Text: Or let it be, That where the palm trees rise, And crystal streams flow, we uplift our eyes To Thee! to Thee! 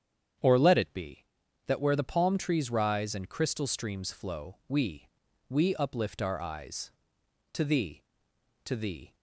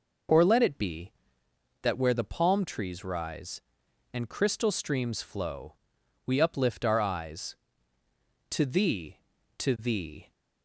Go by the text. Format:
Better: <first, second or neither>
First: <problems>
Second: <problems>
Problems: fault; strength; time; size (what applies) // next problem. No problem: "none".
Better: second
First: starts louder than the rest; strong; until 1.8 s; 8.5 dB // says "we" twice; at 5.4 s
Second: none